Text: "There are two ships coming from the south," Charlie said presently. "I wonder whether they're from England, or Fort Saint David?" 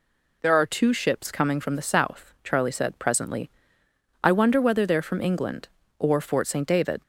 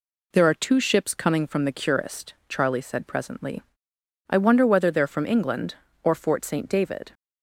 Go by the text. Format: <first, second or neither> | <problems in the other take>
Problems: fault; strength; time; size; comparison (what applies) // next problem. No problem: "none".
first | says "curist" for "south"; at 1.7 s